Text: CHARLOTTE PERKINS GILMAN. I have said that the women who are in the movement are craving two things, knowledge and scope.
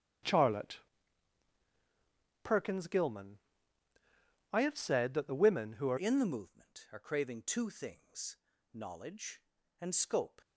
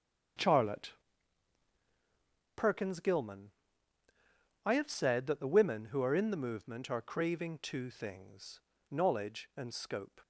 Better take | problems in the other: second | starts louder than the rest; strong; until 2.8 s; 9 dB; strong in the second // pauses between "CHARLOTTE" and "PERKINS"; strong; at 0.7 s; 1.6 s long; strong in the second // changes voice at "in"; from 5.9 s on; 4.5 s long

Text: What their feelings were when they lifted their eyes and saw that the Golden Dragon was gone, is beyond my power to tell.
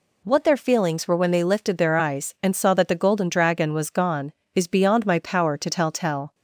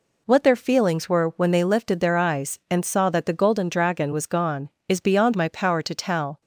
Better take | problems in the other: second | says "tell" twice; at 5.9 s

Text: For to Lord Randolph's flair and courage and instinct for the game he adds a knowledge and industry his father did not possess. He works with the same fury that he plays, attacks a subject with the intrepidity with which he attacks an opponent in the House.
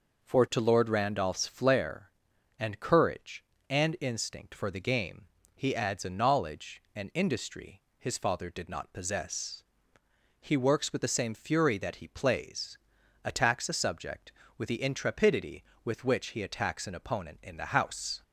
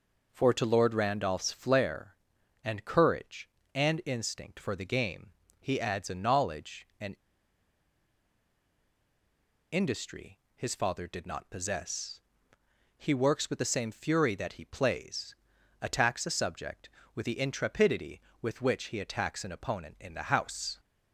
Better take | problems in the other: first | pauses between "game" and "he"; slight; at 5.3 s; 0.28 s long; slight in the first // pauses between "and" and "industry"; strong; at 7.1 s; 2.5 s long // pauses between "industry" and "his"; slight; at 10.3 s; 0.16 s long; slight in the first

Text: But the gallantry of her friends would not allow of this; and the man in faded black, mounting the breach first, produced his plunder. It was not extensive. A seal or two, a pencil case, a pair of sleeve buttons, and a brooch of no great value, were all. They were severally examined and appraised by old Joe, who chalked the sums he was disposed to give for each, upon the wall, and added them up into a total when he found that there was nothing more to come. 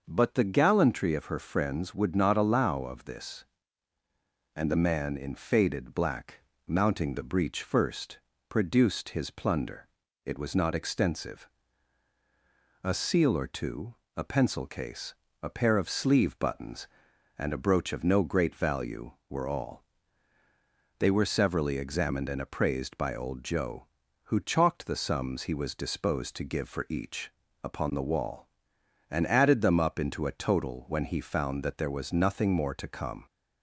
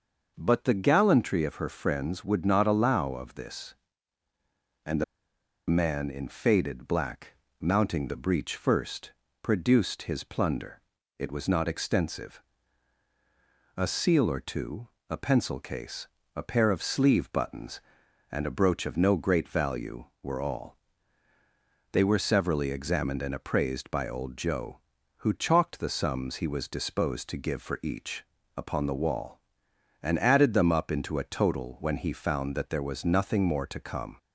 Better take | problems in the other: first | starts louder than the rest; noticeable; until 1.3 s; 6 dB; noticeable in the first // pauses between "the" and "man"; noticeable; at 5.0 s; 0.65 s long

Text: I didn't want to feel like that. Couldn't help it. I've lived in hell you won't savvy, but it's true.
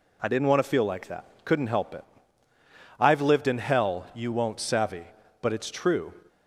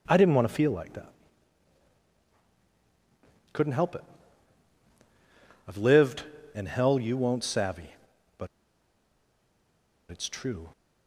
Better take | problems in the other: first | pauses between "but" and "it's"; strong; at 8.4 s; 1.6 s long

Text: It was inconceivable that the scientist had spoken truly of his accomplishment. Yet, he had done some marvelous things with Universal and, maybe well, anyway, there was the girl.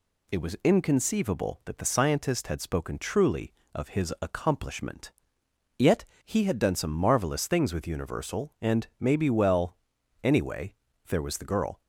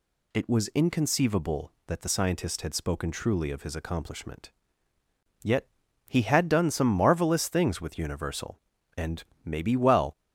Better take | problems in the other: first | stops before "anyway there was the girl"; at 10.1 s

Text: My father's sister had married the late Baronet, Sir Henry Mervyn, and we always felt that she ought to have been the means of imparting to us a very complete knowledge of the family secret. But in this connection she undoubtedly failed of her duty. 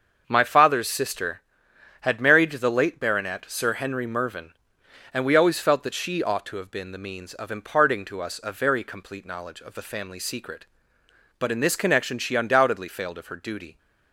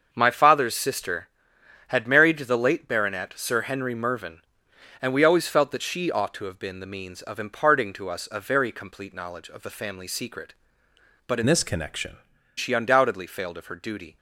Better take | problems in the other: first | starts louder than the rest; until 1.1 s; 6.5 dB; also in the first // changes voice from "this" to "connection"; from 11.4 to 12.1 s; 0.7 s long

